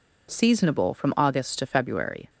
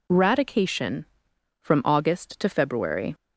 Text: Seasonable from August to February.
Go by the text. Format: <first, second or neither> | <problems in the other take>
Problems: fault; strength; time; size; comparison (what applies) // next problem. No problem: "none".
first | says "Radication" for "Seasonable"; at 0.1 s